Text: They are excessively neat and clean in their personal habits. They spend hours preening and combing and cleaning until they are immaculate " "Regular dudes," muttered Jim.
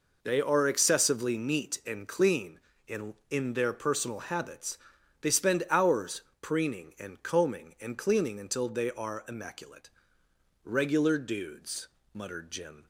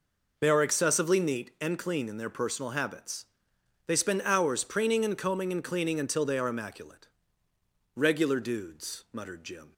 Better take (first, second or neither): second